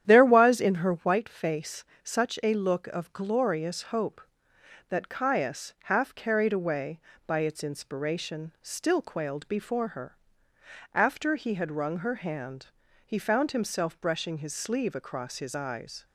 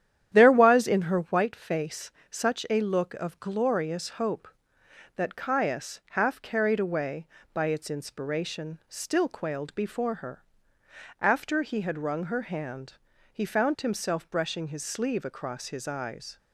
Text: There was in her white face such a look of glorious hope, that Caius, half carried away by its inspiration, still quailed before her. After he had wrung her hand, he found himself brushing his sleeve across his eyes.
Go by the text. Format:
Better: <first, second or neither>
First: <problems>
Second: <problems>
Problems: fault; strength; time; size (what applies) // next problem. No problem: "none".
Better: neither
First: starts louder than the rest; strong; until 1.0 s; 10 dB // pauses between "face" and "such"; slight; at 1.8 s; 0.20 s long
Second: starts louder than the rest; strong; until 1.3 s; 10 dB // pauses between "face" and "such"; slight; at 2.1 s; 0.20 s long